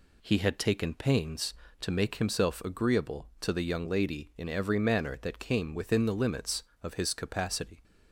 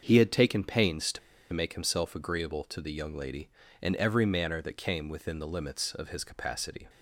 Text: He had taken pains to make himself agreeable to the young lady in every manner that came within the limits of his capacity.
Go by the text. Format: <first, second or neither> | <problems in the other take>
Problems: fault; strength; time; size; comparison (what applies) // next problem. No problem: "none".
first | starts louder than the rest; until 1.0 s; 6.5 dB // pauses between "to" and "make"; slight; at 1.1 s; 0.33 s long